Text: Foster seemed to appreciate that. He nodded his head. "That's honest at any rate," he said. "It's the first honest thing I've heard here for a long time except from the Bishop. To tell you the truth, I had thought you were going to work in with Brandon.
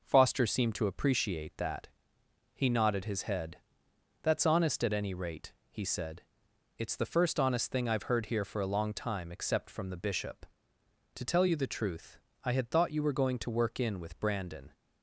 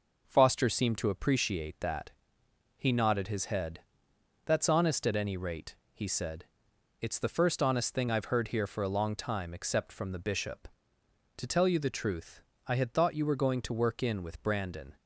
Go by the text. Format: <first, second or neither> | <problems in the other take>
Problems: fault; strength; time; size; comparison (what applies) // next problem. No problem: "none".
neither | none